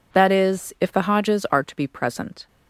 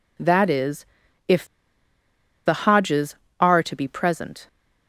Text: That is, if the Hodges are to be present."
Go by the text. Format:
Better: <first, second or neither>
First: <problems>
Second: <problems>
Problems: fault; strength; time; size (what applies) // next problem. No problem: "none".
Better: first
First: none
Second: pauses between "if" and "the"; at 1.4 s; 1.0 s long